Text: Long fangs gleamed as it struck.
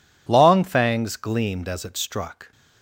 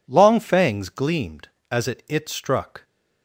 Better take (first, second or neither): first